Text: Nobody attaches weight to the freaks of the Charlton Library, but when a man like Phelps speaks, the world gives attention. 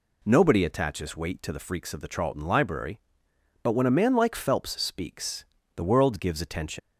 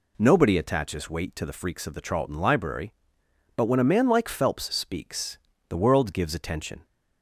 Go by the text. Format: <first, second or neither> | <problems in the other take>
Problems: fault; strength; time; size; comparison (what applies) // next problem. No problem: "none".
second | leaves "attention" unfinished; at 6.7 s; 120 ms